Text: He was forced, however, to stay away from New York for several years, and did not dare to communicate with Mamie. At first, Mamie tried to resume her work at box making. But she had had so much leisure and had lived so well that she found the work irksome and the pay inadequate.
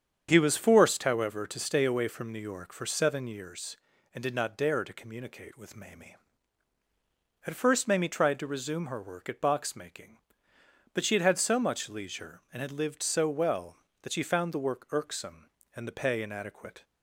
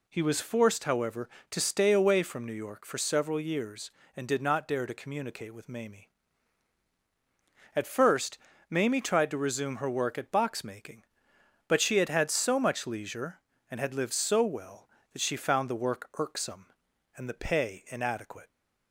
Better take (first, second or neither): second